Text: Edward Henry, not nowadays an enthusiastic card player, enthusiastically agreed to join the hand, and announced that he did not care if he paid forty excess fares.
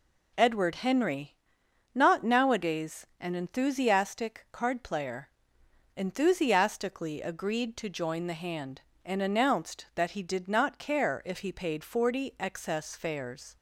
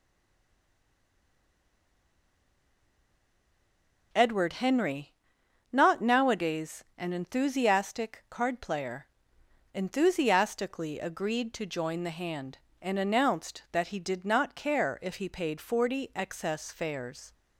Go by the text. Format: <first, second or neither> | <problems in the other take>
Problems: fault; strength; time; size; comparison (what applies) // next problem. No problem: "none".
first | stays silent before the first word; strong; until 4.1 s; 4.1 s long